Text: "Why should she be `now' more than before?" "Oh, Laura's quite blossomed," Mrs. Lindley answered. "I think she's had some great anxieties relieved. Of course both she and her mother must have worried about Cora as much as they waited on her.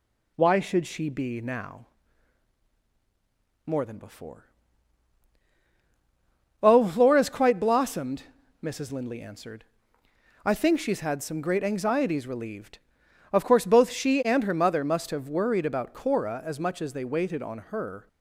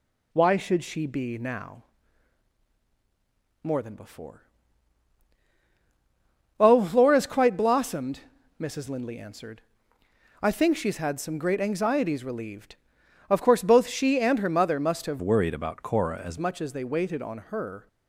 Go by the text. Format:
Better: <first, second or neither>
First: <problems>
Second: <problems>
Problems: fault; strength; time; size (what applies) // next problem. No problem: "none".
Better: first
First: pauses between "now" and "more"; strong; at 1.8 s; 1.8 s long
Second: pauses between "now" and "more"; strong; at 1.8 s; 1.8 s long // changes voice from "worried" to "as"; from 15.2 to 16.3 s; 1.1 s long